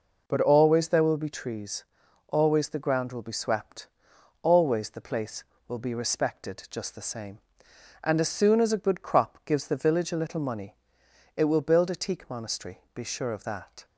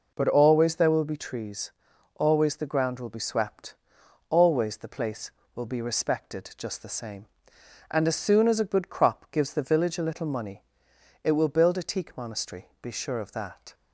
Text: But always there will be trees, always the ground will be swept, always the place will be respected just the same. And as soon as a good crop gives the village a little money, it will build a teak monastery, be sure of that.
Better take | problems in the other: neither | none

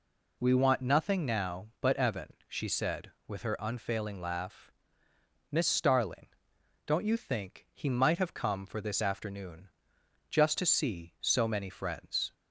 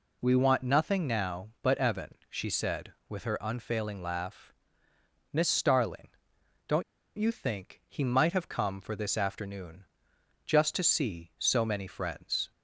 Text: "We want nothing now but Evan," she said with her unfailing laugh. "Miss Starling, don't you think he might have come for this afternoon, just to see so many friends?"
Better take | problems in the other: first | pauses between "don't" and "you"; slight; at 6.8 s; 0.35 s long

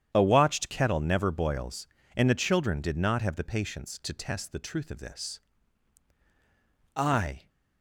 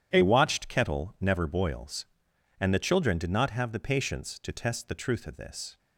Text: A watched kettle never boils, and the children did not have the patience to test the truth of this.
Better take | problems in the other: second | starts louder than the rest; strong; until 1.1 s; 9 dB // goes on to say "I"; from 6.9 s on; 0.52 s long

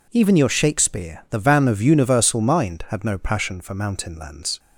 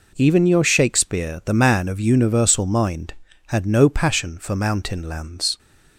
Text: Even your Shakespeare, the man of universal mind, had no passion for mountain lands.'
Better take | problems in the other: second | says "van" for "man"; at 1.3 s

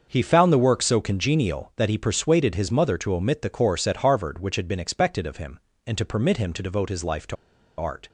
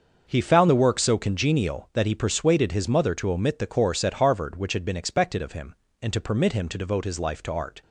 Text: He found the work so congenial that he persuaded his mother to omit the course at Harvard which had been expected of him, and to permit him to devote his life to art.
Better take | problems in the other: second | starts louder than the rest; until 1.1 s; 6.5 dB; also in the second // pauses between "to" and "art"; at 7.3 s; 0.42 s long

